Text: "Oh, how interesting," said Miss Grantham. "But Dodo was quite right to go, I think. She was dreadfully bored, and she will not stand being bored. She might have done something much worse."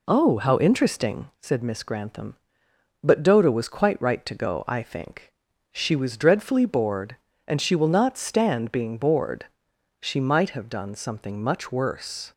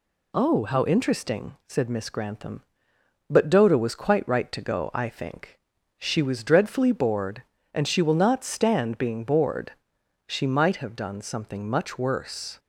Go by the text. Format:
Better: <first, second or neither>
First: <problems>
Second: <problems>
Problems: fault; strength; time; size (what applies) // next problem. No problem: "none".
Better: second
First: starts louder than the rest; slight; until 1.4 s; 3.5 dB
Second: none